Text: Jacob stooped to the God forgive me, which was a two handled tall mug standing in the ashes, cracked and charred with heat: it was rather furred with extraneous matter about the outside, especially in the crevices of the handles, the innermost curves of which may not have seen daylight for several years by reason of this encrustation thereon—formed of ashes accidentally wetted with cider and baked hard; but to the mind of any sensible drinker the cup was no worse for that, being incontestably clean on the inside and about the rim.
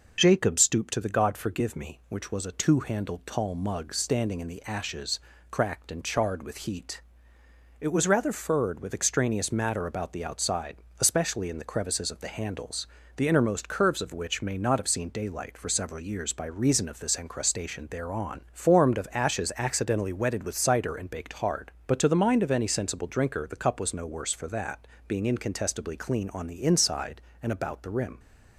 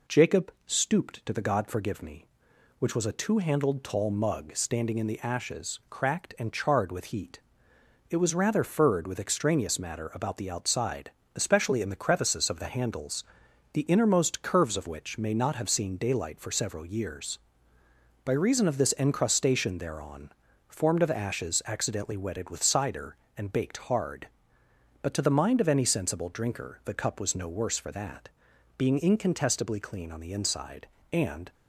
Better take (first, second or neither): first